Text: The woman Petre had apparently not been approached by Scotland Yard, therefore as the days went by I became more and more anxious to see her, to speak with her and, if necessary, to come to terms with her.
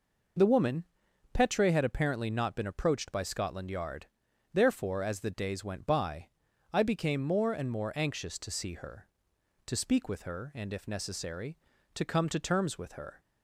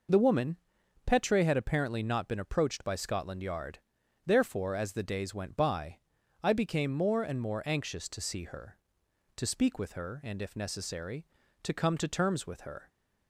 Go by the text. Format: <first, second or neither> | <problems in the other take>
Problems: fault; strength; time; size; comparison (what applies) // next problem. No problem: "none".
neither | pauses between "woman" and "Petre"; noticeable; the same in both // pauses between "by" and "I"; the same in both